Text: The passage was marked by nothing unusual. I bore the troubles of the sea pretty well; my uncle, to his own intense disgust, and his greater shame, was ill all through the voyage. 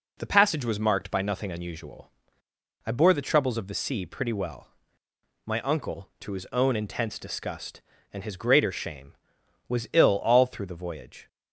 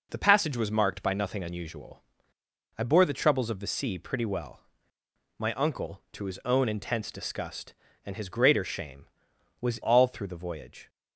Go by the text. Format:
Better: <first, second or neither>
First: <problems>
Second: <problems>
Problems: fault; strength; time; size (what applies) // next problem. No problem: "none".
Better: first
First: none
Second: skips "ill"; at 9.8 s